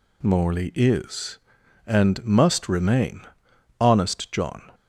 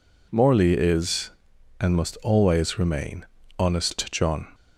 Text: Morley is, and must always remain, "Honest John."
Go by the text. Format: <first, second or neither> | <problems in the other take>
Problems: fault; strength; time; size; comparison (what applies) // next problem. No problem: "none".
second | skips "always"; at 2.6 s